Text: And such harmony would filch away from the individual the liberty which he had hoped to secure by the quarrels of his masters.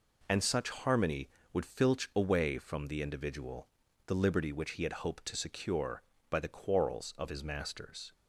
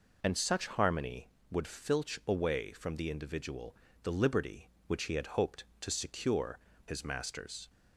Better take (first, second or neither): first